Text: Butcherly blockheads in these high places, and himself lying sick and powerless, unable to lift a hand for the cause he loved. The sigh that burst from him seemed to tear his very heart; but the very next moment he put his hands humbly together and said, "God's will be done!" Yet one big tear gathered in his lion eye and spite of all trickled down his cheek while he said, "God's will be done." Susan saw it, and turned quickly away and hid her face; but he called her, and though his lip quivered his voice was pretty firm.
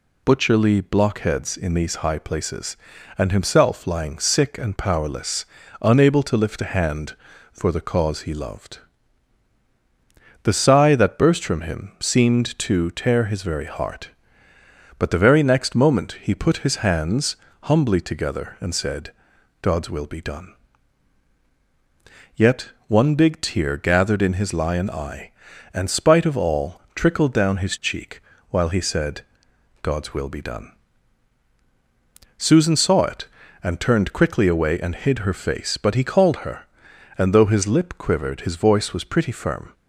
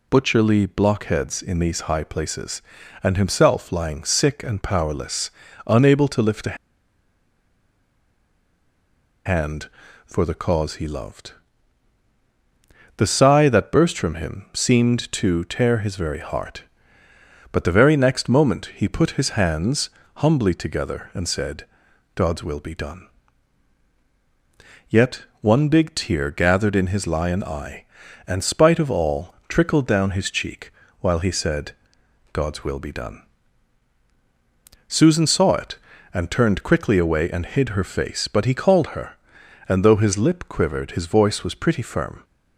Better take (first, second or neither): first